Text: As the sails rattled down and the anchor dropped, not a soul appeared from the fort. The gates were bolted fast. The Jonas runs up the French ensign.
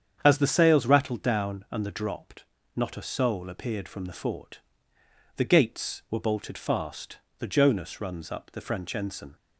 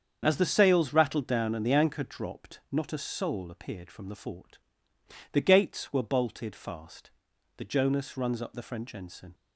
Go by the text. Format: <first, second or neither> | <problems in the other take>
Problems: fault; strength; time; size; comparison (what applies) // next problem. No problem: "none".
second | starts louder than the rest; strong; until 1.2 s; 8 dB; strong in the second // skips "anchor"; at 1.9 s